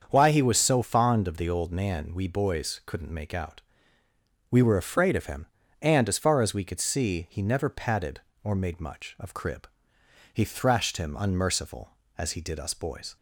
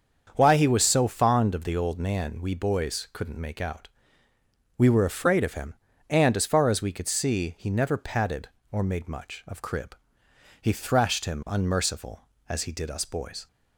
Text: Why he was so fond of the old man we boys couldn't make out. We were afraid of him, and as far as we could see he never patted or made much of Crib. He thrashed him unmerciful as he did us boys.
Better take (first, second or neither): neither